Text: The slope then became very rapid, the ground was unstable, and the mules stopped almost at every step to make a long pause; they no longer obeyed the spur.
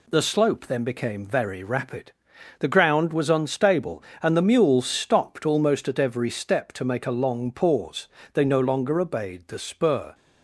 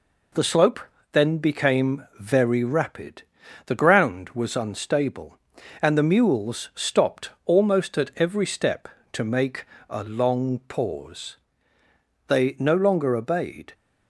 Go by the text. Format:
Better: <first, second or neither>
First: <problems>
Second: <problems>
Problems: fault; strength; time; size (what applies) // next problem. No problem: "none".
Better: first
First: none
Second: pauses between "slope" and "then"; slight; at 0.7 s; 0.32 s long // pauses between "stopped" and "almost"; slight; at 7.2 s; 0.16 s long // pauses between "make" and "a"; slight; at 9.6 s; 0.24 s long // stops before "the spur"; at 13.7 s